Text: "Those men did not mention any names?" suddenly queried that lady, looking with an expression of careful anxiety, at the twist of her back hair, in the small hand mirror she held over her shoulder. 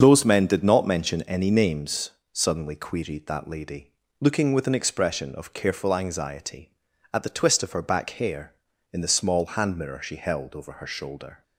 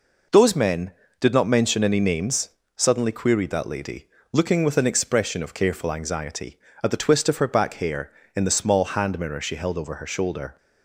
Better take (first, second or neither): second